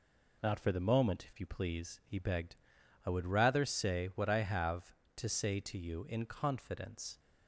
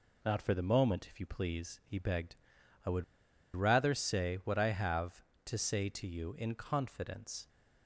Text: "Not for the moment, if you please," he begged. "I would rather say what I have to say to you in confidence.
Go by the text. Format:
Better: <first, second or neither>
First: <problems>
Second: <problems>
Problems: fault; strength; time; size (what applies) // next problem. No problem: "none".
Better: first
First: none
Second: pauses between "would" and "rather"; noticeable; at 3.0 s; 0.51 s long